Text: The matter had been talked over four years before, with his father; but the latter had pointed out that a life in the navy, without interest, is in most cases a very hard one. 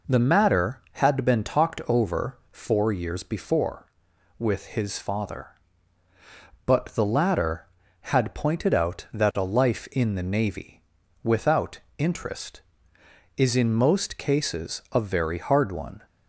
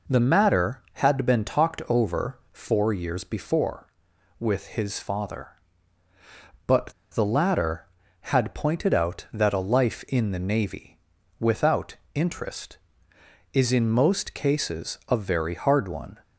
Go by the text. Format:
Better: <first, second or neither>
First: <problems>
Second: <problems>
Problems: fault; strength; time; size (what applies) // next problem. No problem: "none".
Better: first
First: pauses between "without" and "interest"; slight; at 11.7 s; 0.22 s long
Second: pauses between "but" and "the"; slight; at 6.9 s; 0.21 s long // pauses between "without" and "interest"; slight; at 11.9 s; 0.22 s long